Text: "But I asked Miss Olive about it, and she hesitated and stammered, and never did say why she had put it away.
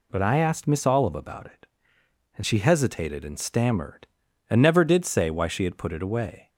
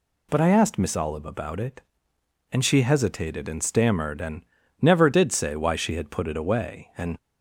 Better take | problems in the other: first | pauses between "and" and "never"; at 4.4 s; 0.38 s long // goes on to say "And"; slight; from 6.9 s on; 0.20 s long

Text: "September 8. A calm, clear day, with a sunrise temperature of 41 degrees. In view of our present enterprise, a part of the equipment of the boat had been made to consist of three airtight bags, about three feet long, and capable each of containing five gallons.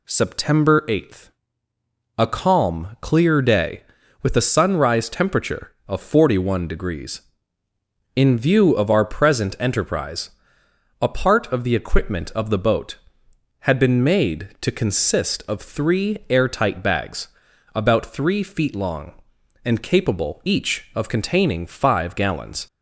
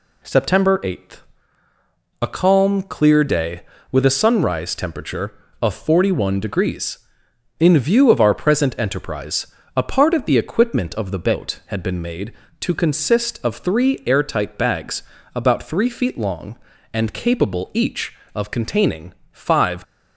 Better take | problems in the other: first | pauses between "containing" and "five"; slight; at 19.1 s; 0.16 s long // stops before "gallons"; at 19.8 s

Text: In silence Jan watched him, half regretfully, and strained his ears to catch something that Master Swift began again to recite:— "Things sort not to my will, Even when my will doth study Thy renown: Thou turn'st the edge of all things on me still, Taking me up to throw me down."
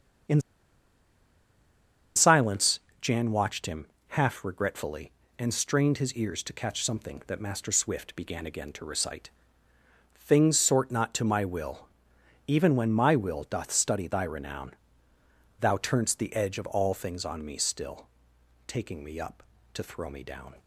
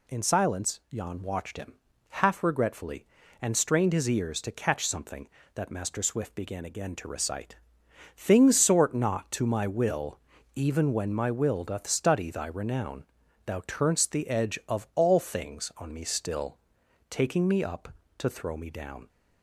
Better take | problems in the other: second | starts louder than the rest; strong; until 3.2 s; 7 dB // pauses between "In" and "silence"; strong; at 0.3 s; 1.7 s long // pauses between "silence" and "Jan"; slight; at 2.7 s; 0.22 s long

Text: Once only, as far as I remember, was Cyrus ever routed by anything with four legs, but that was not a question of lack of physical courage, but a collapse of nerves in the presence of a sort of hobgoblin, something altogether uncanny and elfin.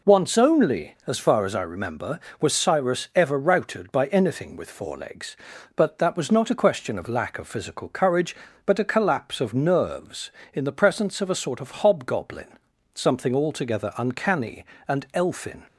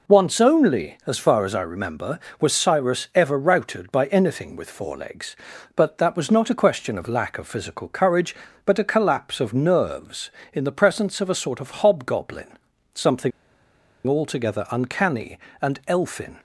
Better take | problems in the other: first | pauses between "something" and "altogether"; noticeable; at 13.3 s; 0.76 s long

